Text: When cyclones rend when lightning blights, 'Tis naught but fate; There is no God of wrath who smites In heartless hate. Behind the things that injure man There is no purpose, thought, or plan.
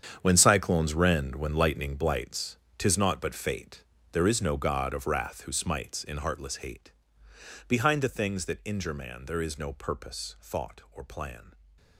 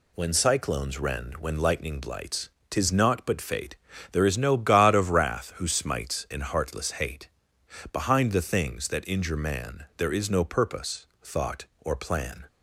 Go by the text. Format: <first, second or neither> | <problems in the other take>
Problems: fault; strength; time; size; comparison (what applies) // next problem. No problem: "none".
second | gets quieter; strong; throughout; 13.5 dB